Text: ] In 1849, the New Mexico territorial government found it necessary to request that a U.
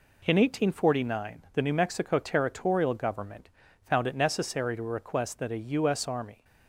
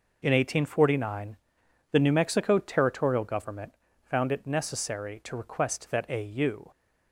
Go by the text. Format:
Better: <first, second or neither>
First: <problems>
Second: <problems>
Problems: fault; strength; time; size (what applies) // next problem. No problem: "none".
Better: second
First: pauses between "government" and "found"; at 3.4 s; 0.40 s long // goes on to say "S Army"; from 5.8 s on; 0.56 s long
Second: pauses between "government" and "found"; slight; at 3.7 s; 0.30 s long